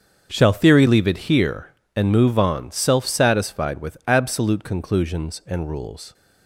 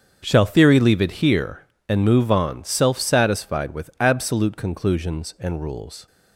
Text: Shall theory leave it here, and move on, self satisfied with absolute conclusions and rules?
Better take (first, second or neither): neither